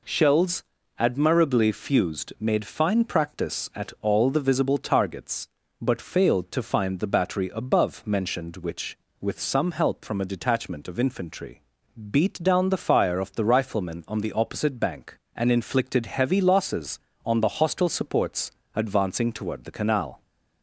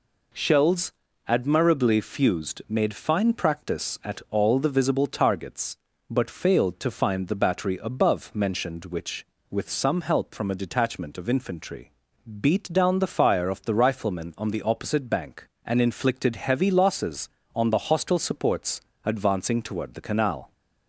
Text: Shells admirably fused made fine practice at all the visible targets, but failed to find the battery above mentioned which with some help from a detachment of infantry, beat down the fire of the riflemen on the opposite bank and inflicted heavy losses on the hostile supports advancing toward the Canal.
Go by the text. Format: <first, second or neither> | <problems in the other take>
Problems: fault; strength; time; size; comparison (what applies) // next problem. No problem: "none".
neither | pauses between "Shells" and "admirably"; the same in both // pauses between "supports" and "advancing"; slight; the same in both